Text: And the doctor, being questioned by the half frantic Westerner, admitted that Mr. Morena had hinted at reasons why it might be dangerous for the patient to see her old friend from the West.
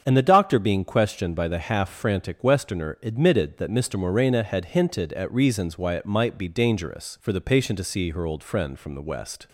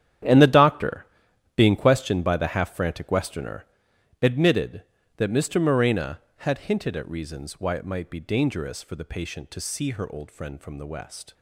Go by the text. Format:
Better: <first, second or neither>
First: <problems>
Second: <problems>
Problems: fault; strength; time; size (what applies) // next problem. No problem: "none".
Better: first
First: starts louder than the rest; strong; until 1.0 s; 7.5 dB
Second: gets quieter; strong; throughout; 14.5 dB // starts louder than the rest; strong; until 1.7 s; 10 dB